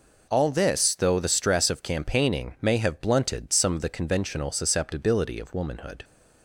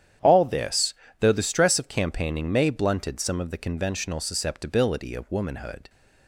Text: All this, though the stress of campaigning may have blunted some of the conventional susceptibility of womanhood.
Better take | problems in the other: first | starts louder than the rest; strong; until 1.5 s; 9.5 dB // skips "have"; at 2.6 s

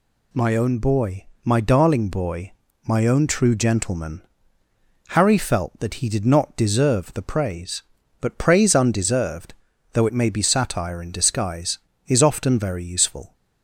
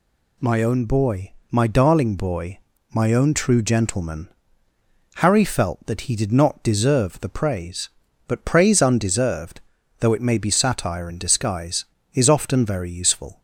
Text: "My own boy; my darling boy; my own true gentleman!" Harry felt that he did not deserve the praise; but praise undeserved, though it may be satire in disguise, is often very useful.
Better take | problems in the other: neither | none

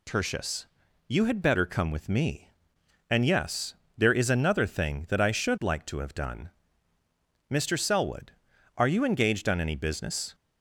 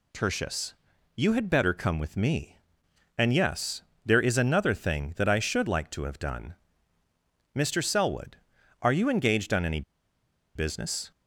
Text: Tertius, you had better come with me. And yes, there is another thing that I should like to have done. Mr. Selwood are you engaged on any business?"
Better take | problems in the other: first | pauses between "any" and "business"; noticeable; at 9.8 s; 0.73 s long

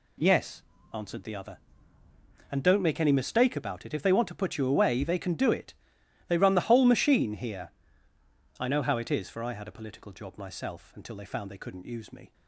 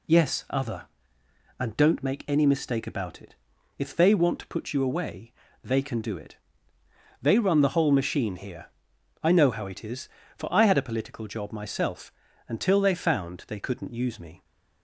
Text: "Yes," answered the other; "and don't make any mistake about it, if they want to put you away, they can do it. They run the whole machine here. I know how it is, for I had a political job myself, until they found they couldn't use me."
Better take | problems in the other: first | skips "answered the"; at 0.4 s

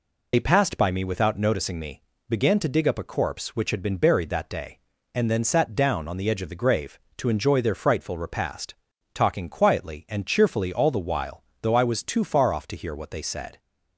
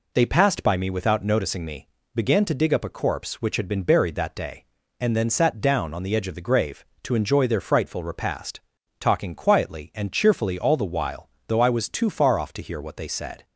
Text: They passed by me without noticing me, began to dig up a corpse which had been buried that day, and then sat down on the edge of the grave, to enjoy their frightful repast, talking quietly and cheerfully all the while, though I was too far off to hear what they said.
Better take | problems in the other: second | loses the start of "They"; at 0.3 s; 50 ms

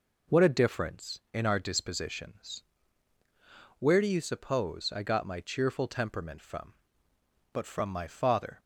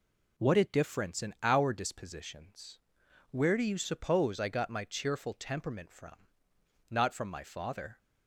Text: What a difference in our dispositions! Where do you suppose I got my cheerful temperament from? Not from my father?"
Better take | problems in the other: second | says "But" for "Not"; at 7.5 s

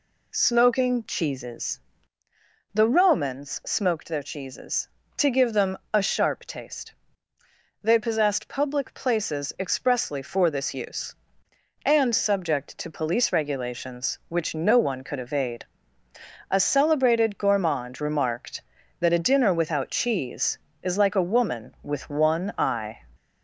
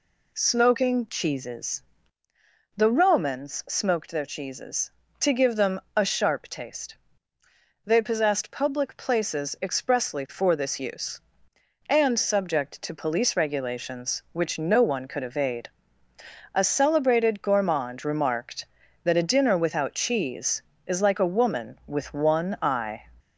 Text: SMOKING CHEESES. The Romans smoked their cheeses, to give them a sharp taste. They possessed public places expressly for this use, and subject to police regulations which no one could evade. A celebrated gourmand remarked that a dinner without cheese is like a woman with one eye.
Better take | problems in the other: neither | pauses between "them" and "a"; slight; the same in both

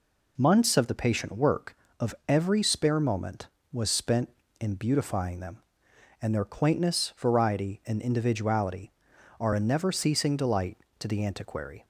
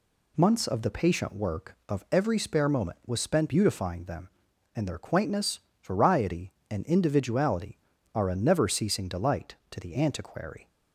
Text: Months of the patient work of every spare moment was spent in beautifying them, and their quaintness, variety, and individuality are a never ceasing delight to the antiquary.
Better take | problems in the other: first | skips "in"; at 3.4 s

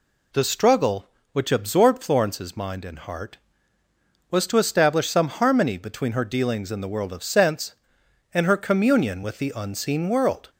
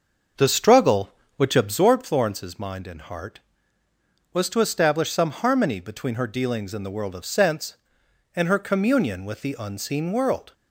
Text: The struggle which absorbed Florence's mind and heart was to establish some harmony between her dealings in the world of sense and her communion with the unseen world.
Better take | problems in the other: first | starts louder than the rest; until 1.9 s; 6.5 dB

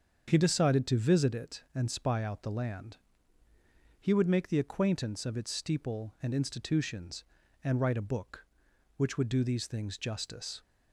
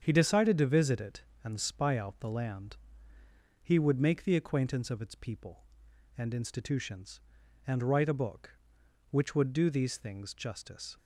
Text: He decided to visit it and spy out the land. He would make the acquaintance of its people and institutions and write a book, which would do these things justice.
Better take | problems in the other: second | starts louder than the rest; until 1.3 s; 7 dB; strong in the second // says "steeple" for "people"; at 5.5 s

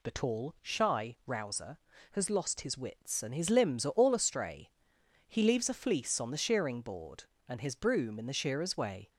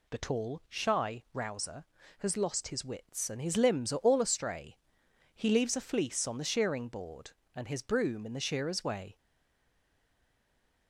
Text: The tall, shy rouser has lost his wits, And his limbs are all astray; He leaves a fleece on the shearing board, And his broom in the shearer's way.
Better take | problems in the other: first | stays silent after the last word; noticeable; from 9.1 s on; 1.7 s long

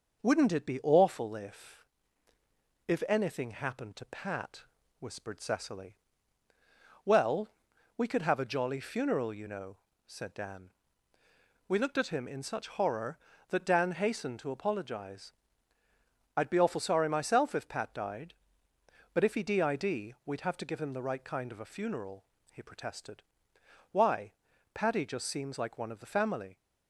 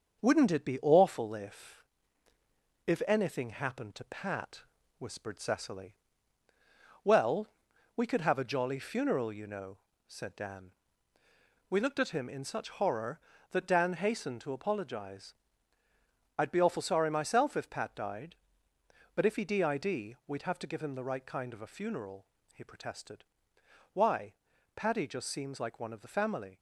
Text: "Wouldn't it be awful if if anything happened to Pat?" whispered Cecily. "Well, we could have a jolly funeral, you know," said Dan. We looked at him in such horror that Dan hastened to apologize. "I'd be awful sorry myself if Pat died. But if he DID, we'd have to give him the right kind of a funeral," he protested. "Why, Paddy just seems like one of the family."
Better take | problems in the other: first | gets quieter; throughout; 3.5 dB // starts louder than the rest; until 1.2 s; 7 dB; noticeable in the first // pauses between "if" and "if"; at 1.8 s; 1.0 s long; also in the first

